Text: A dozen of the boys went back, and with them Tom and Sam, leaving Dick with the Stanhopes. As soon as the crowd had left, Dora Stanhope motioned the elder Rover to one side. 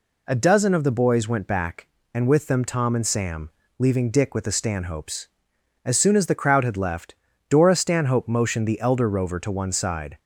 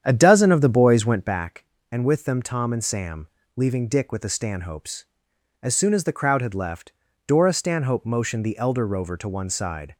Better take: first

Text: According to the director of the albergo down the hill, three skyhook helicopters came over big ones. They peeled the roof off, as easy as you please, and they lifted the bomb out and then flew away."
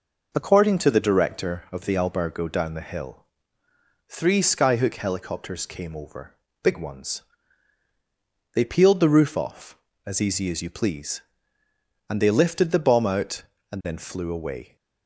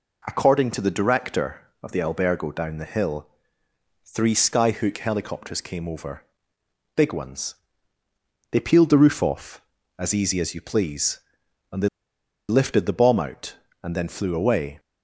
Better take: first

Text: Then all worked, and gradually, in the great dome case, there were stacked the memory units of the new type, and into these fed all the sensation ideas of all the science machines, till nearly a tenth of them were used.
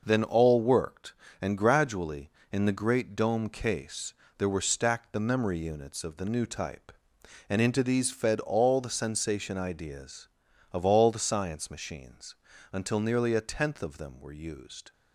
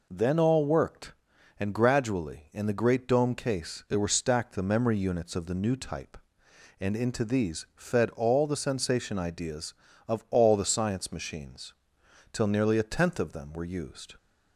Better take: second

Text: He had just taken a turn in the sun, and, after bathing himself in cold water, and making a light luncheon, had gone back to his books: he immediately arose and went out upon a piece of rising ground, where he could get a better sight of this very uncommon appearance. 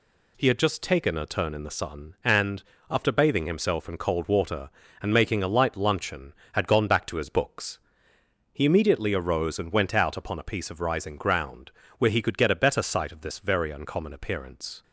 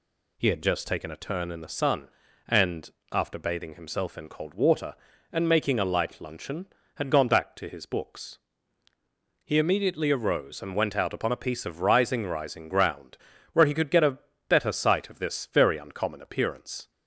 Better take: first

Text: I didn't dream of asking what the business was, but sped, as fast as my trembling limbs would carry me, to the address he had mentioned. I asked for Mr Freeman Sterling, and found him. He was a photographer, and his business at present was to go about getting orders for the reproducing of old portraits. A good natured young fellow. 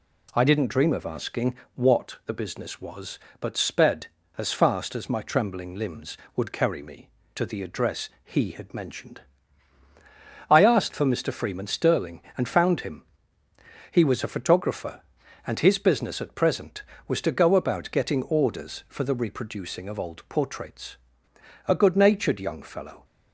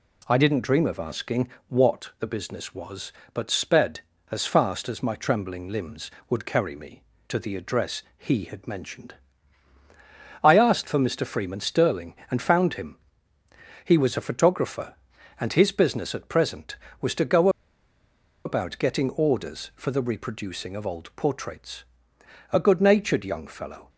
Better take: first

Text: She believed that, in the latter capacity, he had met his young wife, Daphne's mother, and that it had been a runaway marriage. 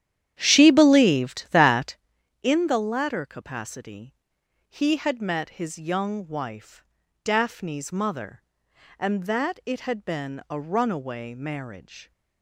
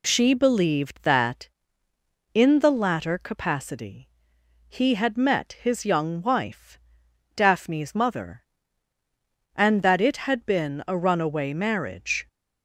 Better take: second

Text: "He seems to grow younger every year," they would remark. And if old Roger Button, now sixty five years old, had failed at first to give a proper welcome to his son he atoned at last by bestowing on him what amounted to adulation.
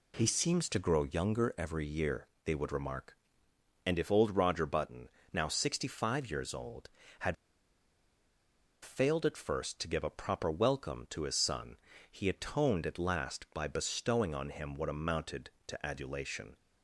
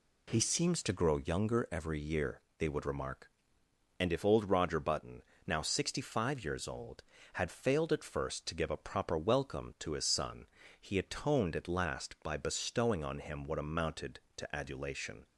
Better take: second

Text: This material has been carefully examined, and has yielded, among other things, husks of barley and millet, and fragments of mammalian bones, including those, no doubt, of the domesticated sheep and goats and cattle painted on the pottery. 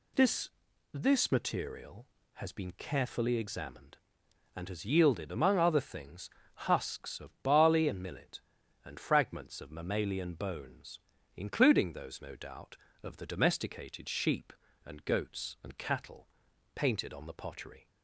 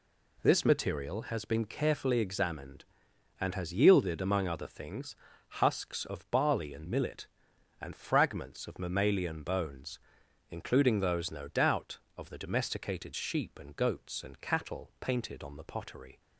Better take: second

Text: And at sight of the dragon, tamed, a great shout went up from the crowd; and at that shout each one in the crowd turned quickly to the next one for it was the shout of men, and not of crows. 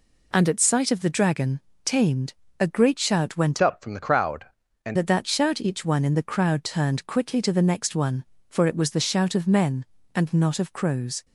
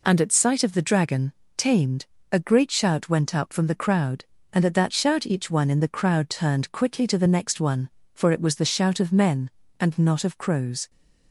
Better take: second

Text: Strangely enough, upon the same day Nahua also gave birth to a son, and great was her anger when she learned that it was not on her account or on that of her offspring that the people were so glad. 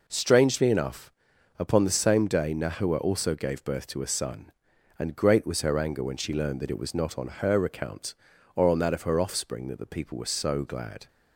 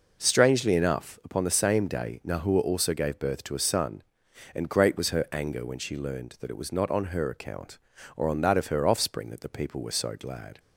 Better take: neither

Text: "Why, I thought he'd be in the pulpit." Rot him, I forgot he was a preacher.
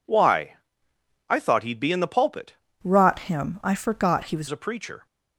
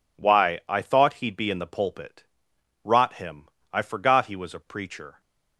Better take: second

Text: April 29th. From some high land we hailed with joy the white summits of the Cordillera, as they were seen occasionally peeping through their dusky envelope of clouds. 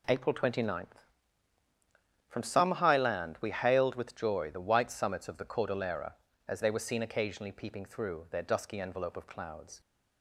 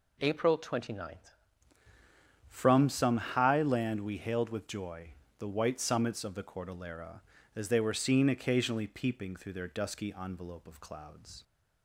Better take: first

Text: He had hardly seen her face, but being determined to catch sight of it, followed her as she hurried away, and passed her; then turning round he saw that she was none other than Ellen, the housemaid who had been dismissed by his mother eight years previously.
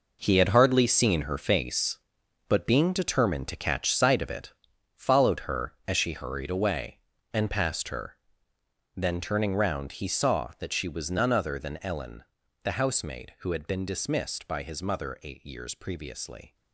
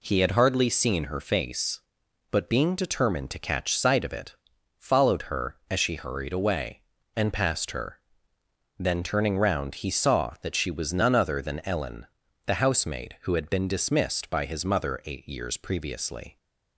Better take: second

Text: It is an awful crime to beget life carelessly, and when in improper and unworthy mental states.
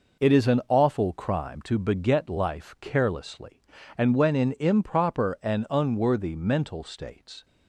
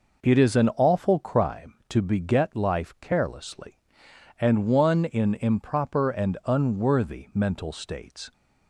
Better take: first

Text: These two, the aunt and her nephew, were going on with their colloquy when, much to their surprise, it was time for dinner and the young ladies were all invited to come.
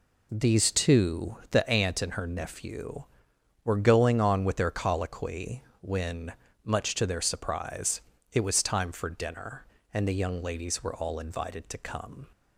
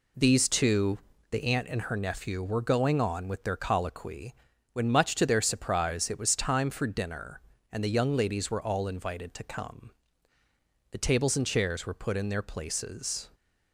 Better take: first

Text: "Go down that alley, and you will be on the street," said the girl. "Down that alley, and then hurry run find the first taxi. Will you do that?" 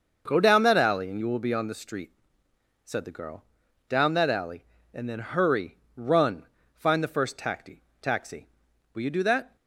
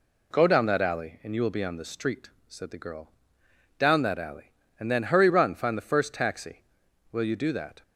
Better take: second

